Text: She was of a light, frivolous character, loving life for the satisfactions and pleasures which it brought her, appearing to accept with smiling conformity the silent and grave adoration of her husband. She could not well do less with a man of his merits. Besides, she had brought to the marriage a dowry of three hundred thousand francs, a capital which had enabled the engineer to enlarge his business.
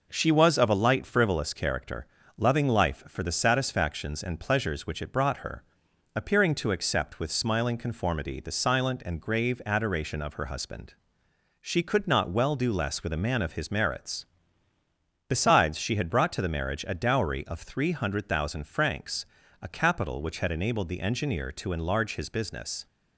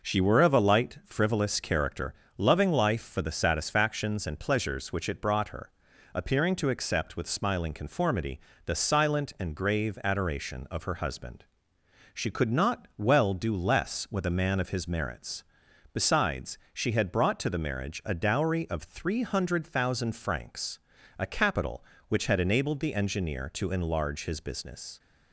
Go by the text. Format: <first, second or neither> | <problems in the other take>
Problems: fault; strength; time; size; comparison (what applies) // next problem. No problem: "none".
first | says "were" for "was"; at 0.1 s // pauses between "conformity" and "the"; slight; at 8.4 s; 0.24 s long